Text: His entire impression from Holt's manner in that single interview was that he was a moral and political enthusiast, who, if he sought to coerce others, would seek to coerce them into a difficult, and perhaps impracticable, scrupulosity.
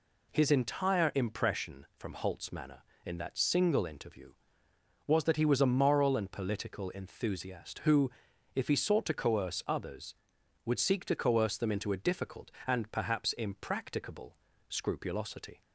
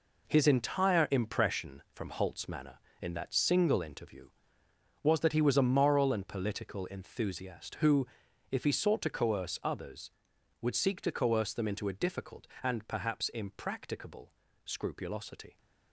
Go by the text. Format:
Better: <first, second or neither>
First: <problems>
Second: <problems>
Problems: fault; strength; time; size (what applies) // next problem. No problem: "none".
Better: first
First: none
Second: gets quieter; strong; throughout; 9.5 dB